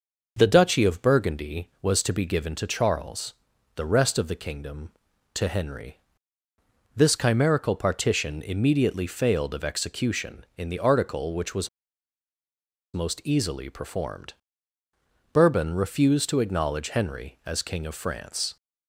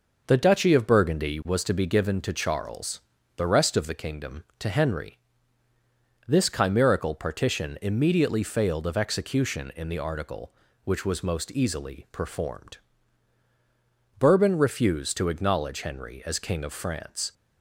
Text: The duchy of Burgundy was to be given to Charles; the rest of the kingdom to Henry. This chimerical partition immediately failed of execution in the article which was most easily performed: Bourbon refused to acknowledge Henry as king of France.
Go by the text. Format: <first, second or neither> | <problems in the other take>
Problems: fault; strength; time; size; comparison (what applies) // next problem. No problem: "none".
second | pauses between "was" and "most"; strong; at 11.6 s; 1.2 s long